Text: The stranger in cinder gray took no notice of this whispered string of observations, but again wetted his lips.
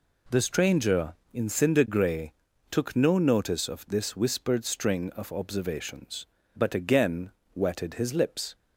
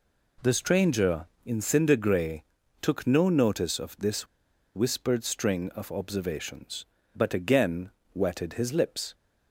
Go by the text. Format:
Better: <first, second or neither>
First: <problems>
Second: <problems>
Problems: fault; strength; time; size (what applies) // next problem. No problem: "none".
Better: first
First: pauses between "gray" and "took"; slight; at 2.3 s; 0.36 s long // pauses between "again" and "wetted"; slight; at 7.3 s; 0.24 s long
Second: pauses between "gray" and "took"; slight; at 2.4 s; 0.36 s long // pauses between "this" and "whispered"; noticeable; at 4.2 s; 0.49 s long // pauses between "again" and "wetted"; slight; at 7.8 s; 0.24 s long